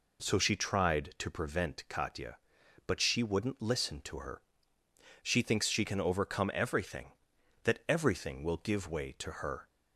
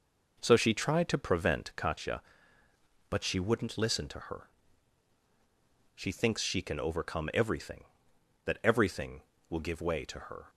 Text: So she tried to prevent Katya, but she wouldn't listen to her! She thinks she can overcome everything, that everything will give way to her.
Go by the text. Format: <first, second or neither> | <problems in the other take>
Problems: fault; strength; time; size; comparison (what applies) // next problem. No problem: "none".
first | starts louder than the rest; noticeable; until 2.1 s; 5 dB